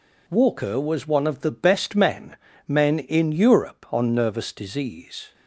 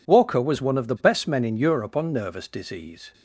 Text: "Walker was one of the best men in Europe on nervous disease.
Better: second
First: says "men" twice; at 2.6 s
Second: none

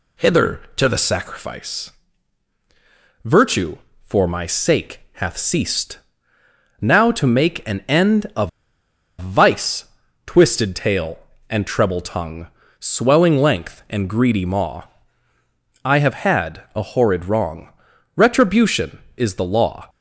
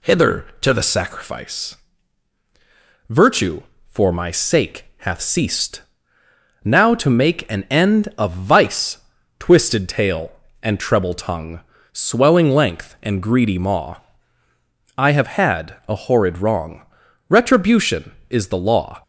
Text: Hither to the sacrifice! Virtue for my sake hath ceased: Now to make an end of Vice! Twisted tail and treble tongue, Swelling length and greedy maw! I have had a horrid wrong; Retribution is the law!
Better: second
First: pauses between "sake" and "hath"; slight; at 5.0 s; 0.20 s long // pauses between "of" and "Vice"; noticeable; at 8.4 s; 0.69 s long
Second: pauses between "sake" and "hath"; slight; at 4.8 s; 0.20 s long

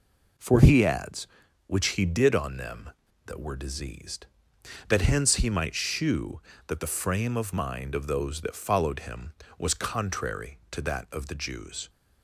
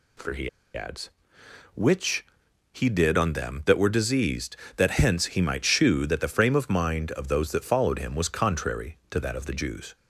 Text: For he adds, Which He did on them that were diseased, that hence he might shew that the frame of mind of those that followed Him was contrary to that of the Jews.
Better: first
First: none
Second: pauses between "he" and "adds"; slight; at 0.4 s; 0.25 s long // pauses between "Which" and "He"; noticeable; at 2.2 s; 0.48 s long

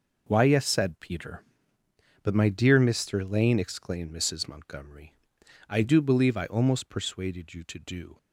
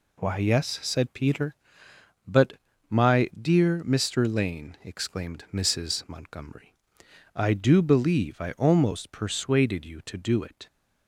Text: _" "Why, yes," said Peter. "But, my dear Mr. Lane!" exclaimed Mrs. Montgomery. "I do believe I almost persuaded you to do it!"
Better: second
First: stops before "it"; at 8.1 s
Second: none

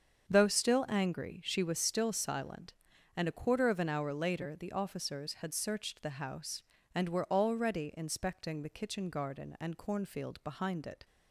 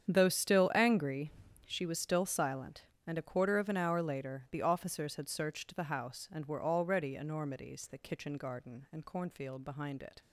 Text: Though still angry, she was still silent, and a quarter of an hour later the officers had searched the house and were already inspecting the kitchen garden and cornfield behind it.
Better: first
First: starts louder than the rest; until 1.3 s; 7 dB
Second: starts louder than the rest; strong; until 1.1 s; 8.5 dB // says "enormities" for "inspecting"; at 7.1 s

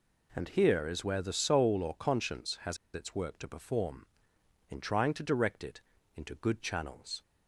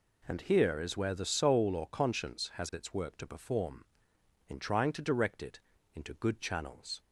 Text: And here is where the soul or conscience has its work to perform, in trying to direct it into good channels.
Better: second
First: pauses between "has" and "its"; slight; at 2.7 s; 0.17 s long // pauses between "it" and "into"; slight; at 5.8 s; 0.34 s long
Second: pauses between "it" and "into"; slight; at 5.6 s; 0.34 s long

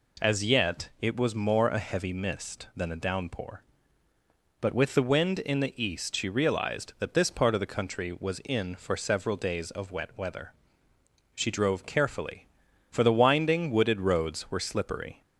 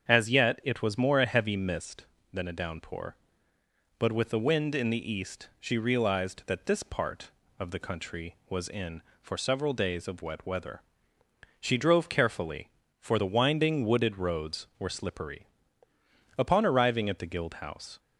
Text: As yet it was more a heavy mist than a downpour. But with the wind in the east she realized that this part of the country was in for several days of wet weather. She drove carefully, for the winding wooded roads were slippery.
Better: first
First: none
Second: starts louder than the rest; strong; until 1.1 s; 7.5 dB // goes on to say "Upon arriving at the Guild House"; from 16.3 s on; 1.6 s long

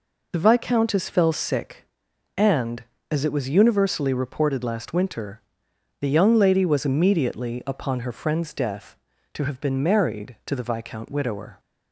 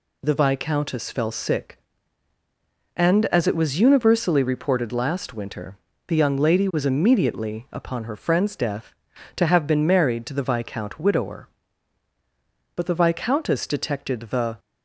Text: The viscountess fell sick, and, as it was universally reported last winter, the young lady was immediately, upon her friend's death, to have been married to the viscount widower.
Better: first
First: none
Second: goes on to say "But the viscountess detected the"; strong; from 12.7 s on; 1.8 s long

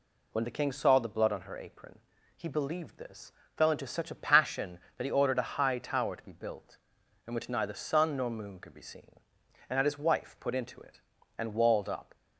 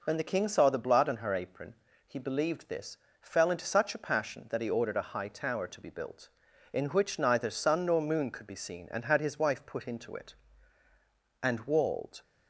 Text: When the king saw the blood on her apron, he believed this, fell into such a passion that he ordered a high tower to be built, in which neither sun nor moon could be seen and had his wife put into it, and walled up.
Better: first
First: none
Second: stops before "up"; at 12.2 s

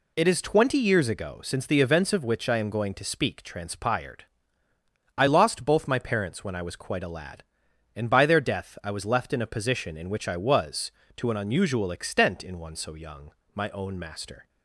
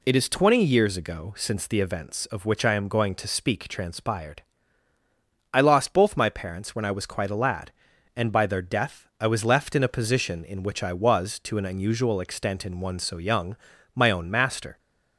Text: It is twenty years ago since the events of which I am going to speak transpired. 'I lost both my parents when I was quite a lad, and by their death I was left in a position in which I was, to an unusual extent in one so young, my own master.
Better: neither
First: none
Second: none

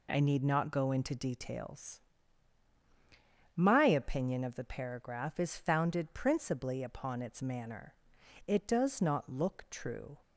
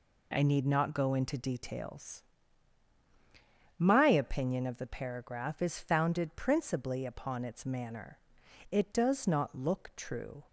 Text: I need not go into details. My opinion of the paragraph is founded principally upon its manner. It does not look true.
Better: neither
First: none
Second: none

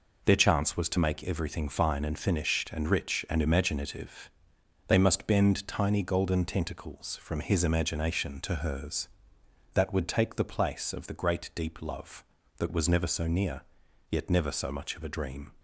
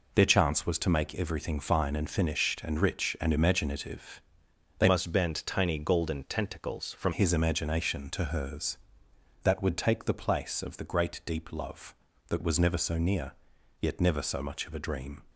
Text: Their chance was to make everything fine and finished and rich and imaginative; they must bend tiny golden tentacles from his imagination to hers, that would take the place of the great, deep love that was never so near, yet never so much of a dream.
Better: first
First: none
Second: changes voice from "must" to "from"; from 4.8 to 7.1 s; 2.3 s long

